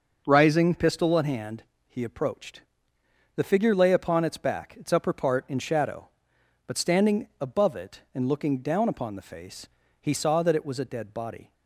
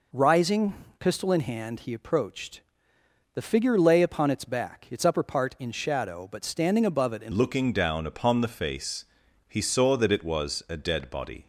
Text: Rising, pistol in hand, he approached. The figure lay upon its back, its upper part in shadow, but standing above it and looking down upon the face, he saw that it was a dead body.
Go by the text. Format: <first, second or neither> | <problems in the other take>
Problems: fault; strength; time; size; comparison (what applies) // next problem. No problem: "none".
first | changes voice at "looking"; from 7.3 s on; 4.1 s long